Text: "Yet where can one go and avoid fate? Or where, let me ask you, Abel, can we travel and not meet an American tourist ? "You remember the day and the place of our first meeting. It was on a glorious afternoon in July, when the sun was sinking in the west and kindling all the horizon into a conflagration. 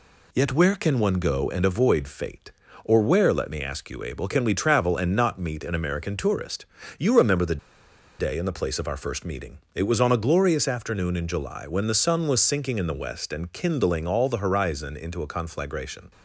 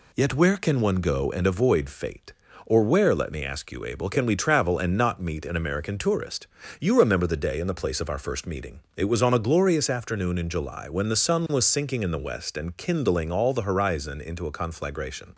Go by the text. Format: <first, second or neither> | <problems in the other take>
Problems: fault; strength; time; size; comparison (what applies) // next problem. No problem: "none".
second | pauses between "the" and "day"; noticeable; at 7.5 s; 0.62 s long